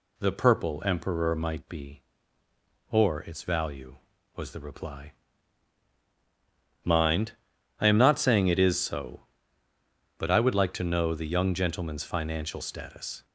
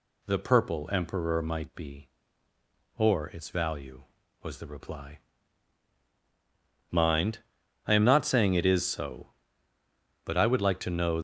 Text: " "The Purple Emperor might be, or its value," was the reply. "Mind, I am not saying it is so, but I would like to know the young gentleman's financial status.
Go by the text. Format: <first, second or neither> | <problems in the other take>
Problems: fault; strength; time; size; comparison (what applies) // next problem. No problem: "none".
first | stops before "the young gentleman's financial status"; at 11.1 s